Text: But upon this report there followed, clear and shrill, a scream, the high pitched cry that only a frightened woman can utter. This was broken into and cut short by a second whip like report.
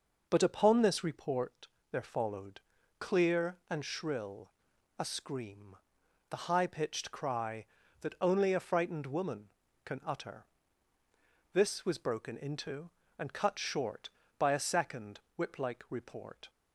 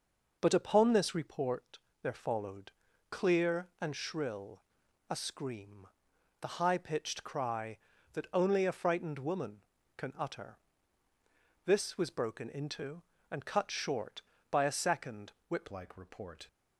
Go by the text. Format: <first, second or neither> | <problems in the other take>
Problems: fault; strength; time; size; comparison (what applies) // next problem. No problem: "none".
first | pauses between "report" and "there"; slight; at 1.7 s; 0.22 s long; slight in the first // pauses between "second" and "whip"; slight; at 15.3 s; 0.18 s long; slight in the first // changes voice at "like"; from 15.6 s on; 0.8 s long